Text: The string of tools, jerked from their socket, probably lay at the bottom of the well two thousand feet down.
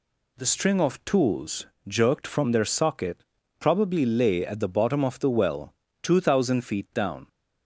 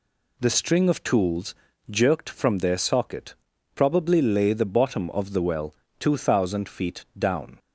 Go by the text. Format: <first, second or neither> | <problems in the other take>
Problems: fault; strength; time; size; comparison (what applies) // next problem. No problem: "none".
first | skips "at"; at 4.5 s // pauses between "well" and "two"; slight; at 5.7 s; 0.24 s long; slight in the first